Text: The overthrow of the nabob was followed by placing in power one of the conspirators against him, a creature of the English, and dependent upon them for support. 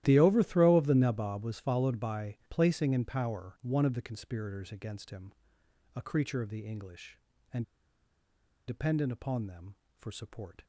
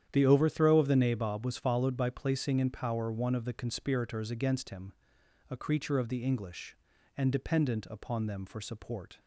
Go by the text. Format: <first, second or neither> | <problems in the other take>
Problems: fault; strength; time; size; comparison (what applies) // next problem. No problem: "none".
second | starts louder than the rest; strong; until 1.0 s; 13.5 dB; strong in the second // pauses between "and" and "dependent"; at 7.6 s; 1.0 s long